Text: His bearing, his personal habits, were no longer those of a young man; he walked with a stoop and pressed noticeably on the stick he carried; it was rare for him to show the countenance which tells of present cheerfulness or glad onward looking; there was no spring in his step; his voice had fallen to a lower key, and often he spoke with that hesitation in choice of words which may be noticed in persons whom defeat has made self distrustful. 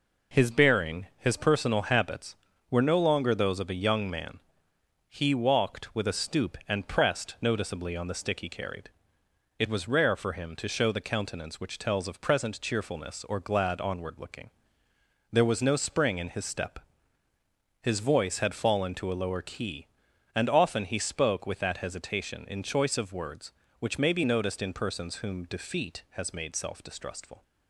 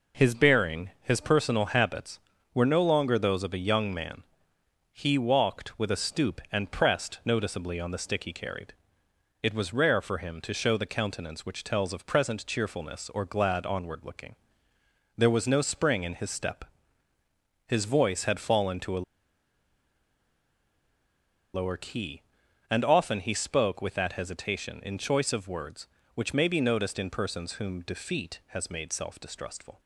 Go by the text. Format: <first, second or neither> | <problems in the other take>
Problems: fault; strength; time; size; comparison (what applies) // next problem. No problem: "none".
first | pauses between "a" and "lower"; strong; at 19.0 s; 2.5 s long